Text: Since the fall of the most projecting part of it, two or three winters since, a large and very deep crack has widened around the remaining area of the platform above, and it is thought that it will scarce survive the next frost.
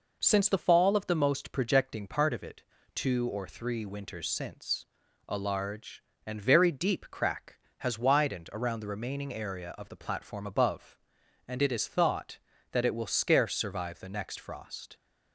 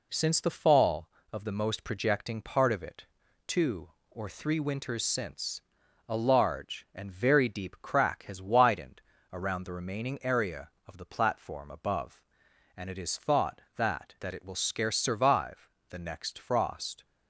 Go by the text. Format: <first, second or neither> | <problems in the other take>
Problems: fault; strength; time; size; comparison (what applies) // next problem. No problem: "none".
first | pauses between "widened" and "around"; slight; at 9.0 s; 0.30 s long // says "that" twice; at 14.1 s // pauses between "survive" and "the"; slight; at 15.6 s; 0.22 s long